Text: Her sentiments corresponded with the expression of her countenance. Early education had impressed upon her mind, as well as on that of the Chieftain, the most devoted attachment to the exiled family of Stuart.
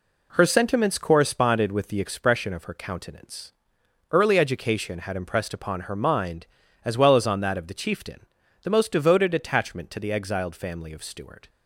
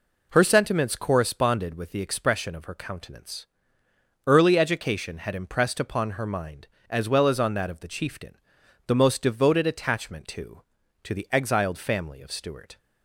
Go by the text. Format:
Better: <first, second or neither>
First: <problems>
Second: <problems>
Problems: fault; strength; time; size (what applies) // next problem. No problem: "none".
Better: first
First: none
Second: says "to" twice; at 11.0 s